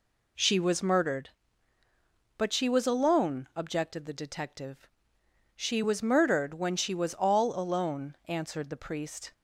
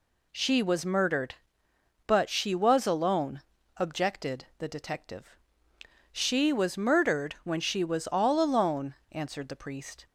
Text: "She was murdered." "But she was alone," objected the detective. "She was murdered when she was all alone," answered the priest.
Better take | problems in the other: neither | none

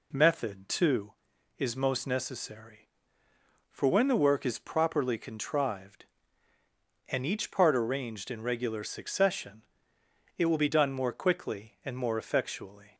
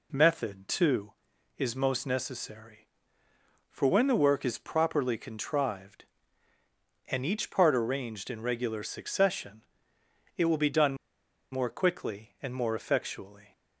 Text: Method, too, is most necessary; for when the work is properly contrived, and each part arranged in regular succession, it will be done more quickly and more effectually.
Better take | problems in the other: first | pauses between "done" and "more"; noticeable; at 10.9 s; 0.56 s long

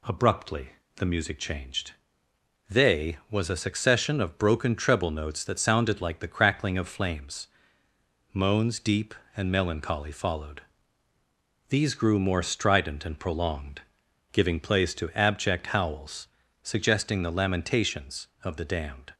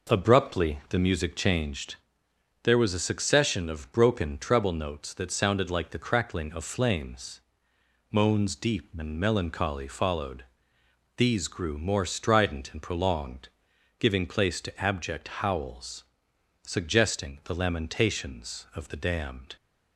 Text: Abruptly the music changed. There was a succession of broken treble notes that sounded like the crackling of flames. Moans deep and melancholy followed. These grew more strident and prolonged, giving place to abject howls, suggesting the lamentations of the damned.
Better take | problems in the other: second | pauses between "Abruptly" and "the"; slight; at 0.6 s; 0.28 s long // says "They" for "There"; at 2.6 s

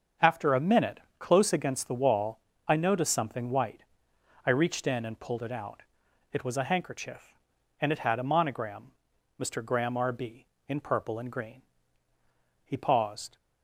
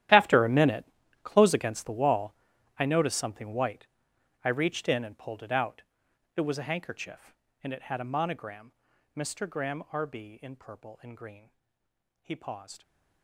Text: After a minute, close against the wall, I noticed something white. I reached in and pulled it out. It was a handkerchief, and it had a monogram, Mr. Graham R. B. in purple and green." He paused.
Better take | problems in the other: first | gets quieter; strong; throughout; 17.5 dB // starts louder than the rest; strong; until 1.4 s; 12 dB; also in the first

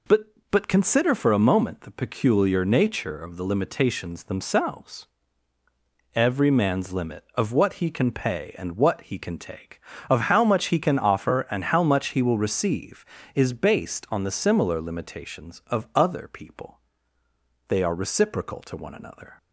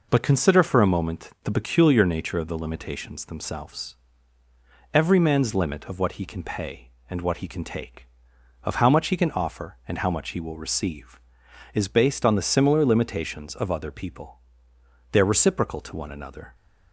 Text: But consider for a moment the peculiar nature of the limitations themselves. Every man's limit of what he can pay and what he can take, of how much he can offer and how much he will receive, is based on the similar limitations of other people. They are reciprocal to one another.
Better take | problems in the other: second | says "But" twice; at 0.4 s

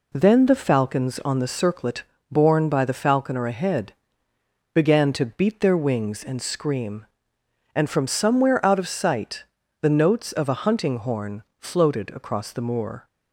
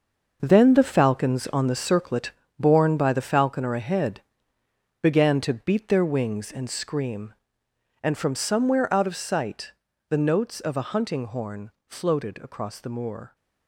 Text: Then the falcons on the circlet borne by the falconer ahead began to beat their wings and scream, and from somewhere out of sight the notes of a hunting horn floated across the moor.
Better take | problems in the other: first | gets quieter; strong; throughout; 11 dB // pauses between "circlet" and "borne"; slight; at 2.3 s; 0.28 s long; slight in the first // pauses between "ahead" and "began"; noticeable; at 4.2 s; 0.82 s long; noticeable in the first // pauses between "sight" and "the"; slight; at 9.7 s; 0.36 s long; slight in the first // pauses between "horn" and "floated"; slight; at 11.7 s; 0.18 s long; slight in the first

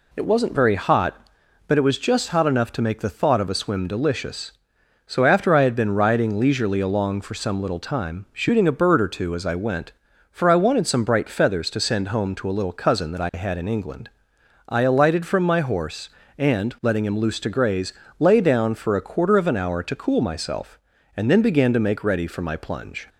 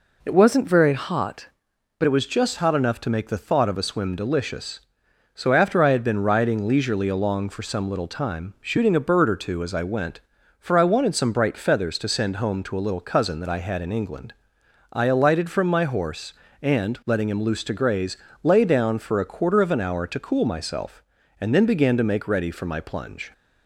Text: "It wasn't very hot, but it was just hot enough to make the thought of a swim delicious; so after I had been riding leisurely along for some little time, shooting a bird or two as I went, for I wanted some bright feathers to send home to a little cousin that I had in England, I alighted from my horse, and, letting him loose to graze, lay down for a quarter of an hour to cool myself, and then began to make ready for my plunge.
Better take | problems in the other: first | changes voice from "wasn't" to "but"; from 0.3 to 2.0 s; 1.7 s long

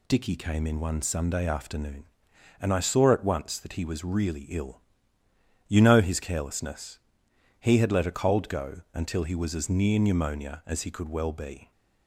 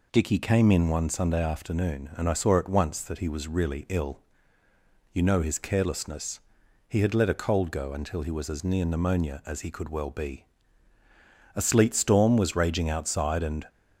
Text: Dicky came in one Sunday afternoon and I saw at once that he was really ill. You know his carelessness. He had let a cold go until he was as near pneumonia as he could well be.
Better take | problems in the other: first | goes on to say "A sleet storm was raging outside and"; strong; from 11.5 s on; 2.1 s long

